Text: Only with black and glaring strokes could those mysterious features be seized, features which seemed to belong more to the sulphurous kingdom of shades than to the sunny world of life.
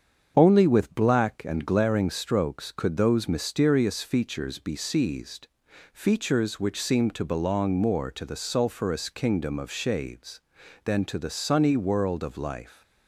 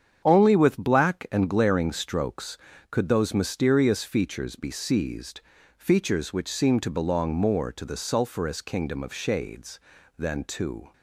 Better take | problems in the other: first | starts louder than the rest; strong; until 1.2 s; 8 dB; strong in the first // stops before "the sunny world of life"; at 10.9 s

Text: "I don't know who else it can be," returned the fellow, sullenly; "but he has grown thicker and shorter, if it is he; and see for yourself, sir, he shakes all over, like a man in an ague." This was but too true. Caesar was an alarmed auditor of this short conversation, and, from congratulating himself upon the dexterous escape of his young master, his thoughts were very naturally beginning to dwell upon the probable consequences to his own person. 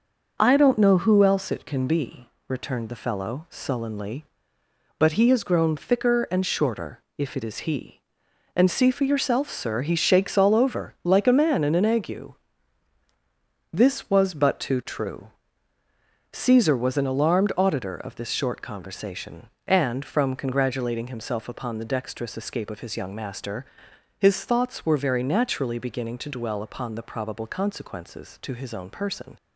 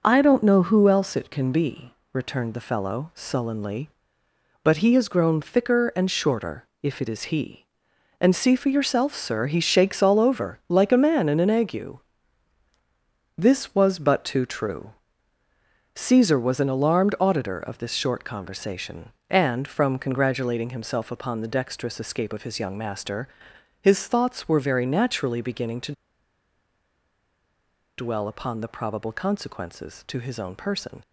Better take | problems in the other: first | pauses between "to" and "dwell"; strong; at 25.9 s; 2.0 s long

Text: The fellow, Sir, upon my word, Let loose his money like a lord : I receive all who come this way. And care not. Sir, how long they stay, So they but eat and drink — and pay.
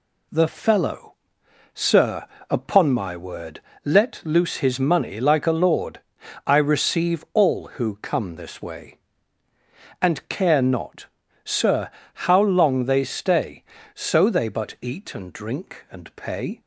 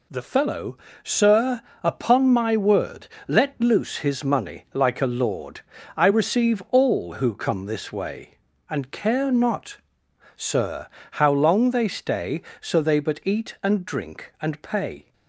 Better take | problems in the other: neither | none

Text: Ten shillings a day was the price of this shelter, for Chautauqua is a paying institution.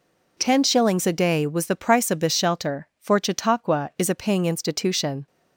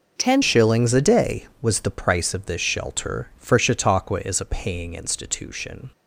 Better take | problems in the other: first | changes voice at "shillings"; from 0.4 s on; 5.5 s long

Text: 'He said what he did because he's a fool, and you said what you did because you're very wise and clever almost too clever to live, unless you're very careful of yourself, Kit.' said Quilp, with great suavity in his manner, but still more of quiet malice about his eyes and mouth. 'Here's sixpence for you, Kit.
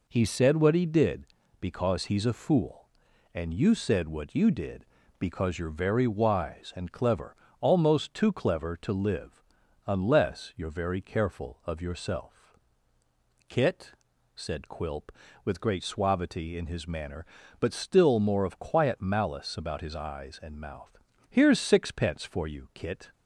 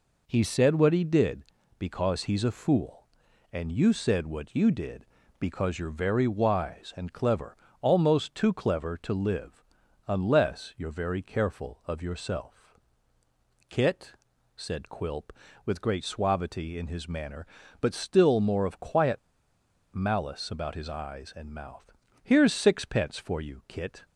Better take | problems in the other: first | pauses between "clever" and "almost"; slight; at 7.5 s; 0.26 s long; slight in the first // pauses between "quiet" and "malice"; noticeable; at 19.1 s; 0.73 s long

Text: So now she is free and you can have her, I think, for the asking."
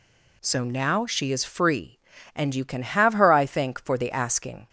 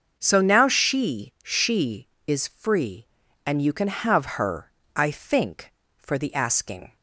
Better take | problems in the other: first | starts louder than the rest; until 1.1 s; 6 dB // says "she" twice; at 1.4 s

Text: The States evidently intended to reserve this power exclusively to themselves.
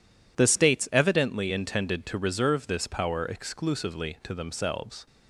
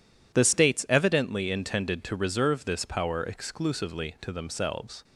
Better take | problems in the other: neither | none

